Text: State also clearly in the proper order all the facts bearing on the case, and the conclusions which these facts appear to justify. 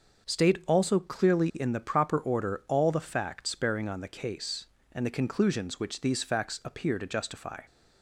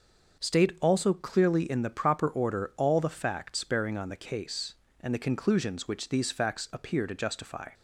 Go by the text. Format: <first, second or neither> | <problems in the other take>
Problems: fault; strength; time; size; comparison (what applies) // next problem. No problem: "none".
neither | none